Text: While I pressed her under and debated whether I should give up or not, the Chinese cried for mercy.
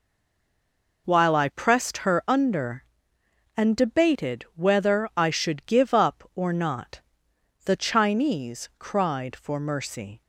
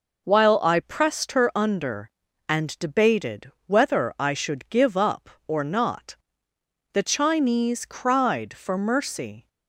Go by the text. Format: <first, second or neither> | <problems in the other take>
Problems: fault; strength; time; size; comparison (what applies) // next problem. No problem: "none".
second | stays silent before the first word; until 1.0 s; 1.0 s long